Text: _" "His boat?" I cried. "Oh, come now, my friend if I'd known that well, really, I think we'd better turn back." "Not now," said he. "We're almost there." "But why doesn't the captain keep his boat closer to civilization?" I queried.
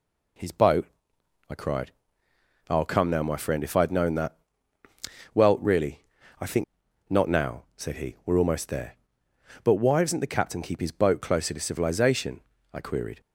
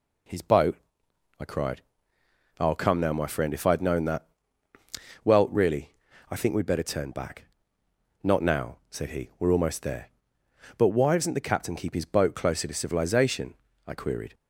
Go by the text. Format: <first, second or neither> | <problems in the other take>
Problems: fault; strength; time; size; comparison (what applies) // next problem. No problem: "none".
second | pauses between "that" and "well"; noticeable; at 4.3 s; 0.96 s long; noticeable in the second // skips "we'd better turn back"; at 6.8 s